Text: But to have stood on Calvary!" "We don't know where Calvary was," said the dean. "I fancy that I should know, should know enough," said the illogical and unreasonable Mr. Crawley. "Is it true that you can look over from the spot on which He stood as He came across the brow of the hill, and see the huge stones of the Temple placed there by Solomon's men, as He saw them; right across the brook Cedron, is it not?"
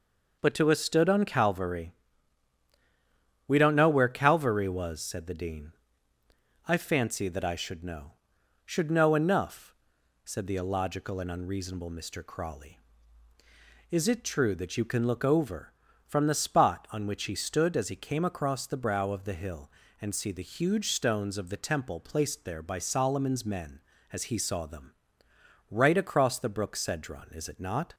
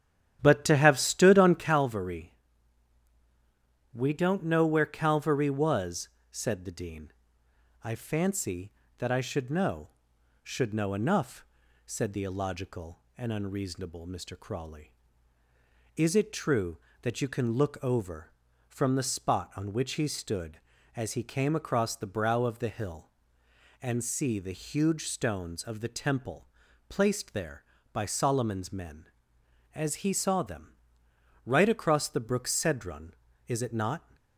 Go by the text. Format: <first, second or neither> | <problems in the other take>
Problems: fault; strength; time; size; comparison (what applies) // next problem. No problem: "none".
first | starts louder than the rest; strong; until 1.8 s; 10.5 dB // pauses between "Temple" and "placed"; at 26.4 s; 0.40 s long